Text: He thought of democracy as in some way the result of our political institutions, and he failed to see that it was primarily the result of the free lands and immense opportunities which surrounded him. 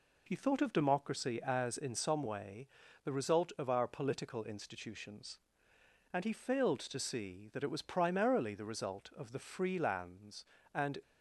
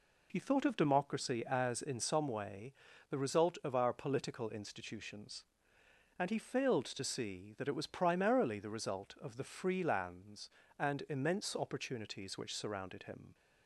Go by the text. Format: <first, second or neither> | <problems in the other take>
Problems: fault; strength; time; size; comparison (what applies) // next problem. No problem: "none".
second | pauses between "way" and "the"; slight; at 2.6 s; 0.36 s long; slight in the second // stops before "immense opportunities which surrounded him"; at 11.0 s